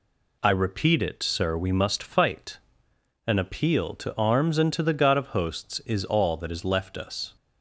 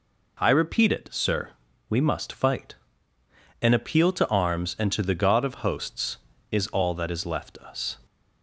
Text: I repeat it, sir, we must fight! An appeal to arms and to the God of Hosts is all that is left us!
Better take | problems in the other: neither | none

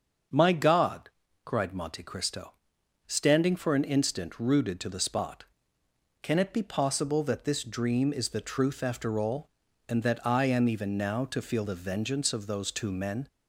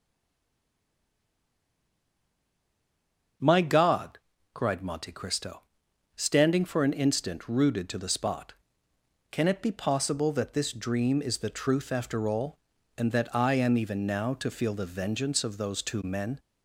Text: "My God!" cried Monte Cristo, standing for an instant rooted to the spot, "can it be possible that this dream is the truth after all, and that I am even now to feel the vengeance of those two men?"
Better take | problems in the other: first | stays silent before the first word; strong; until 3.3 s; 3.3 s long // starts louder than the rest; until 4.7 s; 7 dB; also in the first

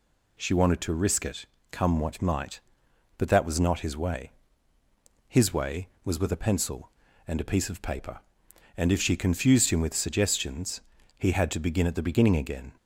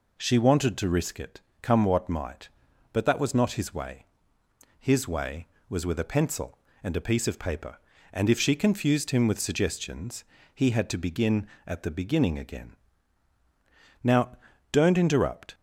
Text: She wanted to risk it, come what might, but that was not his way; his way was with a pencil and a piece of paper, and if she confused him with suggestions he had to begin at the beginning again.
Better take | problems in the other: first | pauses between "suggestions" and "he"; slight; at 10.2 s; 0.28 s long; also in the first // goes on to say "Now don't interrupt"; from 14.0 s on; 1.5 s long

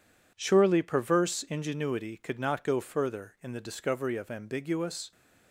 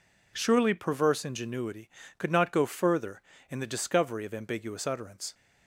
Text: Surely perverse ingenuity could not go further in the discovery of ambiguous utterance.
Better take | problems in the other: second | stops before "utterance"; at 5.1 s

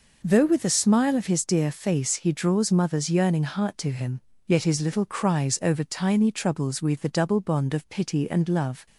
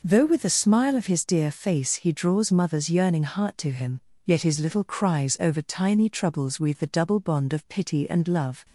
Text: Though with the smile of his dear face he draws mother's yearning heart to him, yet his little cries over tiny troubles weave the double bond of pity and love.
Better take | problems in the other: neither | none

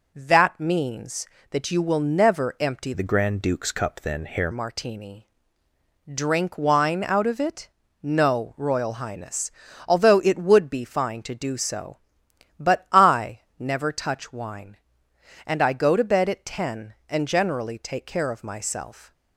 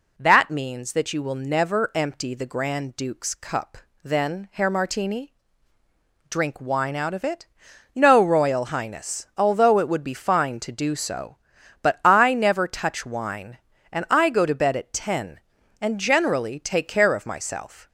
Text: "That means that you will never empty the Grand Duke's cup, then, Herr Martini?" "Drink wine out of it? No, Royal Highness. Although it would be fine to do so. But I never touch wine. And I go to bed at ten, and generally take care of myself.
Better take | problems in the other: second | changes voice from "the" to "Herr"; from 2.9 to 4.4 s; 1.5 s long // pauses between "I" and "never"; slight; at 13.4 s; 0.18 s long

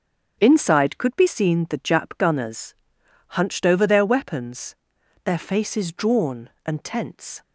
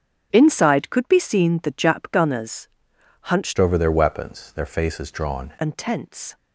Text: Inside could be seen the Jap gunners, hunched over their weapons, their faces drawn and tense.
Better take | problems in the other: first | starts louder than the rest; strong; until 1.3 s; 8 dB; strong in the first // changes voice from "over" to "drawn"; from 3.5 to 5.5 s; 2.0 s long

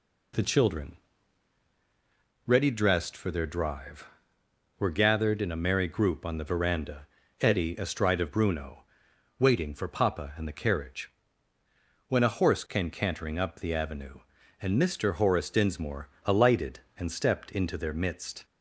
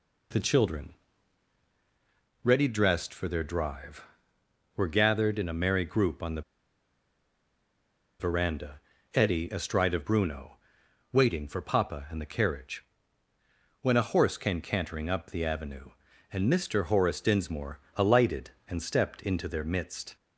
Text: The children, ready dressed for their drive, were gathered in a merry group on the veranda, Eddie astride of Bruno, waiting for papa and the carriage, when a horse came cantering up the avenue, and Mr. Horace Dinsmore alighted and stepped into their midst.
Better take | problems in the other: first | pauses between "the" and "veranda"; strong; at 6.4 s; 1.7 s long // pauses between "Dinsmore" and "alighted"; slight; at 17.7 s; 0.18 s long; slight in the first

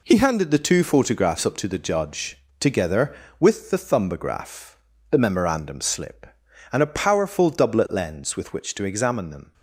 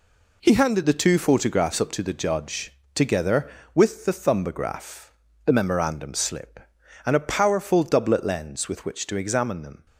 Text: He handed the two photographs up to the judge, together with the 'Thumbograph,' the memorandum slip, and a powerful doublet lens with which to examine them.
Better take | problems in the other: neither | none

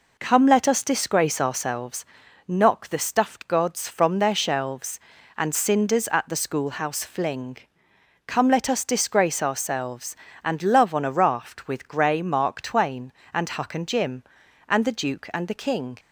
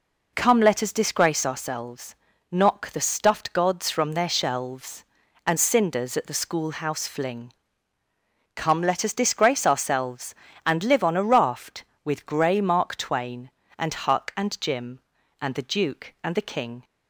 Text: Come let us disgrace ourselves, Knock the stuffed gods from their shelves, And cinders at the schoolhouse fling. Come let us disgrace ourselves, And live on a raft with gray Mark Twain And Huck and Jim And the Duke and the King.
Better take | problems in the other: second | says "love" for "live"; at 10.6 s

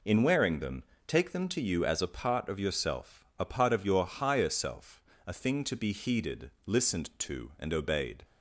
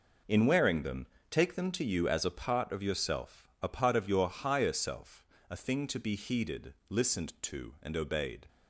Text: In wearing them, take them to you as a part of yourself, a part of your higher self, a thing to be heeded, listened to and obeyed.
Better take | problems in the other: first | gets quieter; strong; throughout; 10 dB

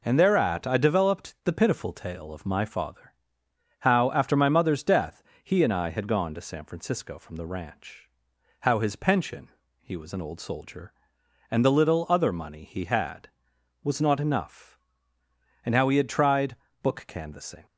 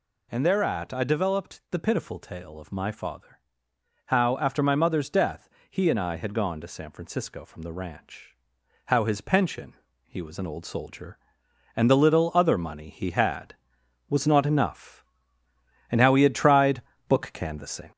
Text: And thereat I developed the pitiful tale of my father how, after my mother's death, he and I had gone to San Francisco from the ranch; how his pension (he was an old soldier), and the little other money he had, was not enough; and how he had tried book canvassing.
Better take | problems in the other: first | gets louder; slight; throughout; 2.5 dB // pauses between "father" and "how"; noticeable; at 3.3 s; 0.70 s long; noticeable in the first // pauses between "tried" and "book"; slight; at 16.8 s; 0.26 s long; slight in the first

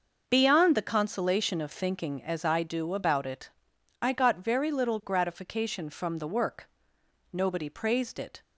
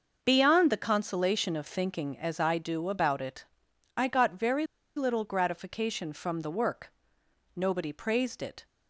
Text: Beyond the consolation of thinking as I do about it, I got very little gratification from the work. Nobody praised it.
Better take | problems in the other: first | starts louder than the rest; noticeable; until 1.2 s; 6 dB; noticeable in the first // pauses between "very" and "little"; slight; at 4.6 s; 0.30 s long

